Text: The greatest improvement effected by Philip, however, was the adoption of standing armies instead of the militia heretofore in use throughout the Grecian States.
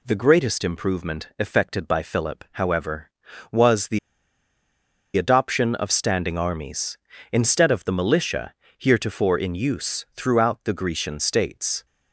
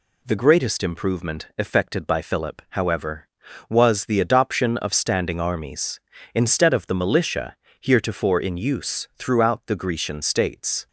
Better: second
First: pauses between "the" and "adoption"; at 3.9 s; 1.1 s long // pauses between "militia" and "heretofore"; slight; at 8.5 s; 0.24 s long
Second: pauses between "militia" and "heretofore"; slight; at 7.5 s; 0.24 s long

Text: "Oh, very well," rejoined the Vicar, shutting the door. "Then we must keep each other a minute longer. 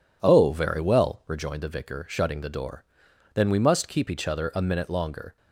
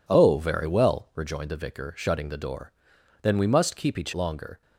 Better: first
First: none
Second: skips "other a minute"; at 4.1 s

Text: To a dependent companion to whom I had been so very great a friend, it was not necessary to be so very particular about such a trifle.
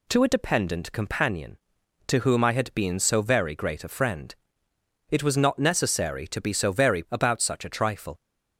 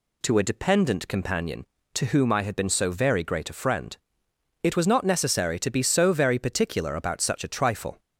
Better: second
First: skips "particular"; at 7.0 s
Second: none

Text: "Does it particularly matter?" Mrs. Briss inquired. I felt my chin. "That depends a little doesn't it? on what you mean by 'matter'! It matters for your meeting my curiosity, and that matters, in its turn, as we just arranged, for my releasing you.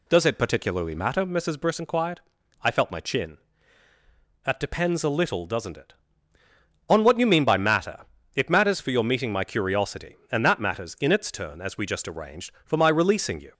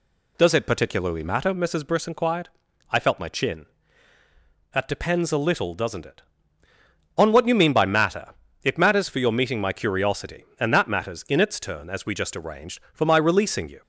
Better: neither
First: none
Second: none

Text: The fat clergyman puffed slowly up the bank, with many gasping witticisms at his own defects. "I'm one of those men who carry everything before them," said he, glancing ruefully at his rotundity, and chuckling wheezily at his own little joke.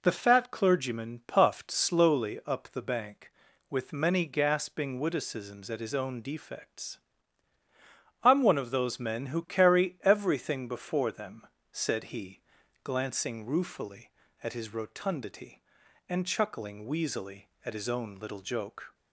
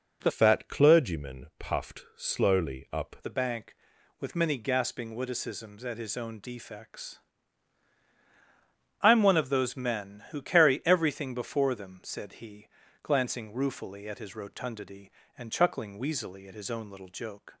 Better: first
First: none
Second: changes voice from "fat" to "up"; from 0.2 to 3.1 s; 2.9 s long

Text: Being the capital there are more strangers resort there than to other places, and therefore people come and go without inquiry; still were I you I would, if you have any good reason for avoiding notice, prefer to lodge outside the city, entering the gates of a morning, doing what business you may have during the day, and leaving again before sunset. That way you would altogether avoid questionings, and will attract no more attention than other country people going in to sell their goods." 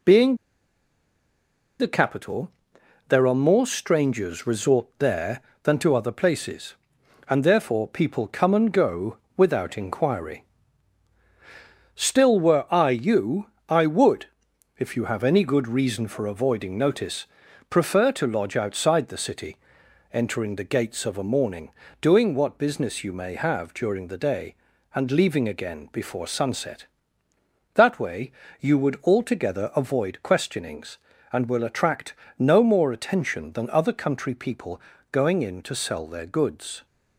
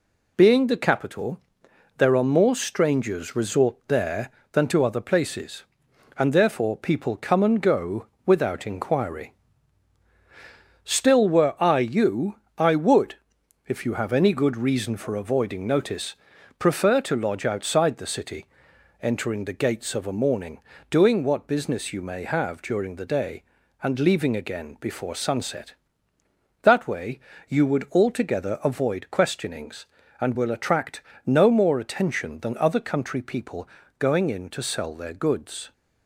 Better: second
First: pauses between "Being" and "the"; strong; at 0.3 s; 1.4 s long // pauses between "capital" and "there"; noticeable; at 2.5 s; 0.58 s long // pauses between "go" and "without"; slight; at 9.1 s; 0.20 s long // pauses between "you" and "I"; slight; at 13.4 s; 0.24 s long // pauses between "way" and "you"; slight; at 28.3 s; 0.30 s long // pauses between "attract" and "no"; slight; at 32.1 s; 0.26 s long // pauses between "people" and "going"; slight; at 34.8 s; 0.30 s long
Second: pauses between "capital" and "there"; noticeable; at 1.3 s; 0.58 s long // pauses between "go" and "without"; slight; at 8.0 s; 0.20 s long // pauses between "you" and "I"; slight; at 12.3 s; 0.24 s long // pauses between "way" and "you"; slight; at 27.1 s; 0.30 s long // pauses between "attract" and "no"; slight; at 31.0 s; 0.26 s long // pauses between "people" and "going"; slight; at 33.6 s; 0.30 s long

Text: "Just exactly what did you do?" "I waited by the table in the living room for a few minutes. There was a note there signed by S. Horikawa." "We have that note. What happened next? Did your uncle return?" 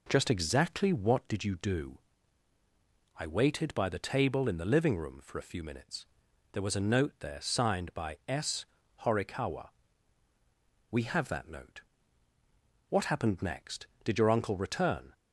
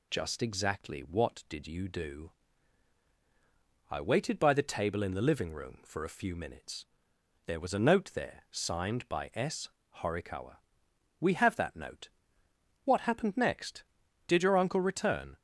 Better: neither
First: none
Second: none

